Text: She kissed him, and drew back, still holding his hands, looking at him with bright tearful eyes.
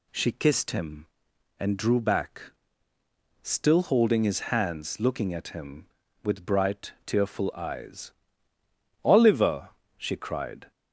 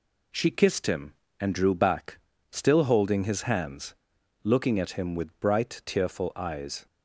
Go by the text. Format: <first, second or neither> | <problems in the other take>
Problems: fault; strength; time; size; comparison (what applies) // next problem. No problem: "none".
second | goes on to say "Oliver she cried"; from 9.0 s on; 1.6 s long